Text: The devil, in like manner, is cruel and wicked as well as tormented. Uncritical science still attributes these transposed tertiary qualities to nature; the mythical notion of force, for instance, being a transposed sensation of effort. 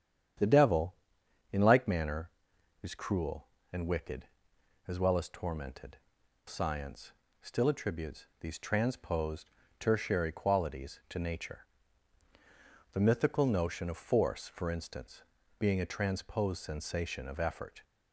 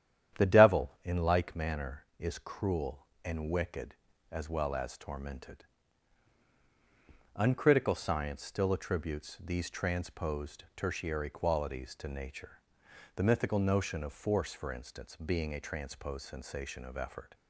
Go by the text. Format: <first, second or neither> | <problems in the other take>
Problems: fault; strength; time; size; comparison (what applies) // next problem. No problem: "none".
second | starts louder than the rest; strong; until 1.9 s; 9 dB; strong in the second // skips "Uncritical"; at 6.2 s // pauses between "science" and "still"; slight; at 7.1 s; 0.30 s long // pauses between "attributes" and "these"; slight; at 8.2 s; 0.16 s long // pauses between "transposed" and "tertiary"; slight; at 9.5 s; 0.28 s long